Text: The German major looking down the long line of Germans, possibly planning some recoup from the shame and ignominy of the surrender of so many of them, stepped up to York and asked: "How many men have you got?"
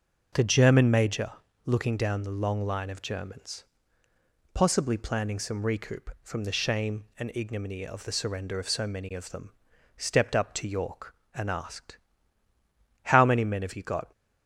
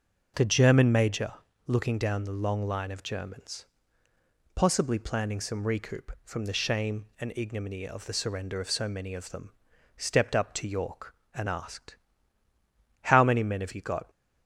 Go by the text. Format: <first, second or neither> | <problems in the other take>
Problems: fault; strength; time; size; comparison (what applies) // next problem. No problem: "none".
neither | pauses between "major" and "looking"; slight; the same in both